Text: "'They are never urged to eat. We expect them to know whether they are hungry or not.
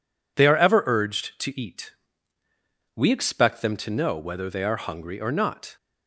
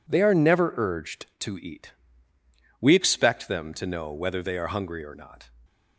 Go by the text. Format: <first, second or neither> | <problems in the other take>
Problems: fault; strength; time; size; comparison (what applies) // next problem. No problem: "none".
second | says "ever" for "never"; at 0.5 s